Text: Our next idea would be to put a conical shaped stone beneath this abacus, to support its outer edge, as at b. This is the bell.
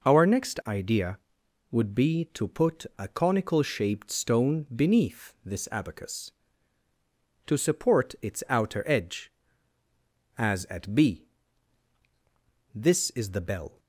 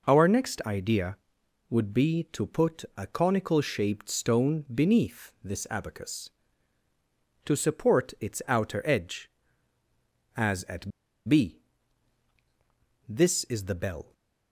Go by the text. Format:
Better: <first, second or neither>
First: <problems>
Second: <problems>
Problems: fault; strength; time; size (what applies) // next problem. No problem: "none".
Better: first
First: none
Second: pauses between "at" and "b"; at 10.9 s; 0.37 s long